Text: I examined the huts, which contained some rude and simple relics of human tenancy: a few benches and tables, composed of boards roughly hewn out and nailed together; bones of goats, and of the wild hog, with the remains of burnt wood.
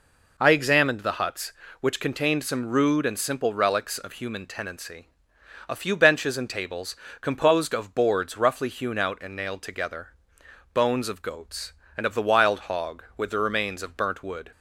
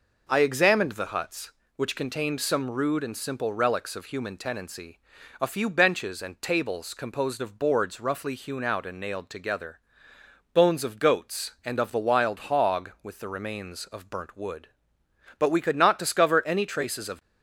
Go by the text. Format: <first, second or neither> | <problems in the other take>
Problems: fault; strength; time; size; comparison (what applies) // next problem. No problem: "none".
first | goes on to say "But we could not discover any traces of"; strong; from 15.3 s on; 1.8 s long